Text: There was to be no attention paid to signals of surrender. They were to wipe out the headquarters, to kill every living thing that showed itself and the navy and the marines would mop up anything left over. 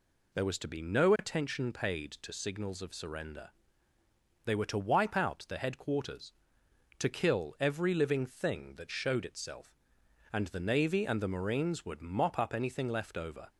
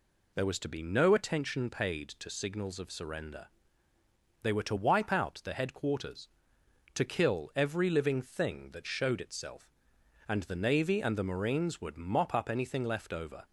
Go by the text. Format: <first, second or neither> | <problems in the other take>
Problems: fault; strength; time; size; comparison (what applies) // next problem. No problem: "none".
neither | none